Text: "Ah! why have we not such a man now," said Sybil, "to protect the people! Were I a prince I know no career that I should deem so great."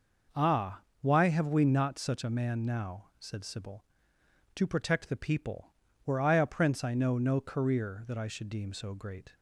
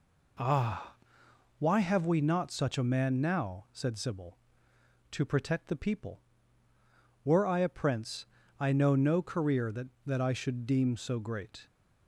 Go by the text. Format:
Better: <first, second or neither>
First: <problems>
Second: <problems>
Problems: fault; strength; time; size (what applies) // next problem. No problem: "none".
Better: first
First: none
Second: pauses between "prince" and "I"; slight; at 8.2 s; 0.36 s long // says "that" twice; at 10.0 s